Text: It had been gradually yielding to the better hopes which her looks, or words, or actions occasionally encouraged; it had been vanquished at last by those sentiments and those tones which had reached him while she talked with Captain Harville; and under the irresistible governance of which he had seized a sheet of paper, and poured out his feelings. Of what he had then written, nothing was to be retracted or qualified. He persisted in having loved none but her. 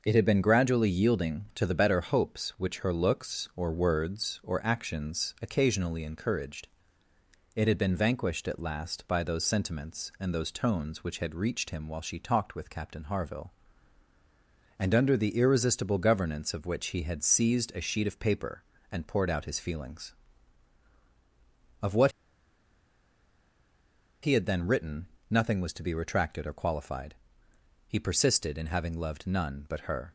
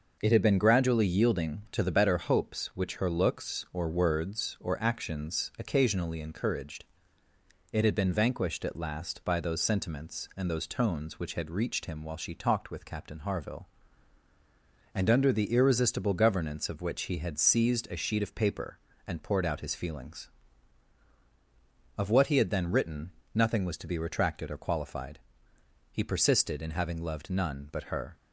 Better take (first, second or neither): second